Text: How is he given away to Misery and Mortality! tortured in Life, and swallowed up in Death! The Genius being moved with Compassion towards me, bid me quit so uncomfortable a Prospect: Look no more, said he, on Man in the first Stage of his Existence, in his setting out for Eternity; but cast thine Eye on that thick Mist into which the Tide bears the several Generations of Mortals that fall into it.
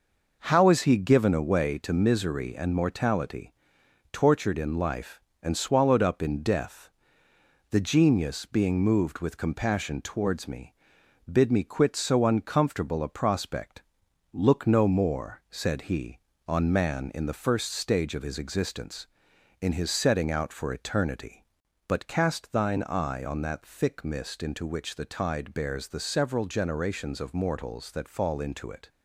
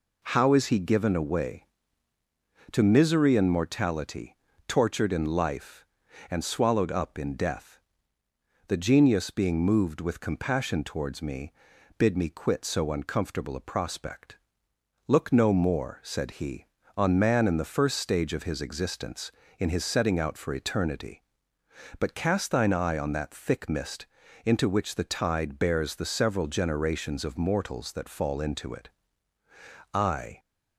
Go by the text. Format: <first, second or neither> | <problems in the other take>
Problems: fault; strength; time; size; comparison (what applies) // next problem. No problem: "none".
first | pauses between "Mist" and "into"; at 24.0 s; 0.38 s long // goes on to say "I"; slight; from 29.9 s on; 0.46 s long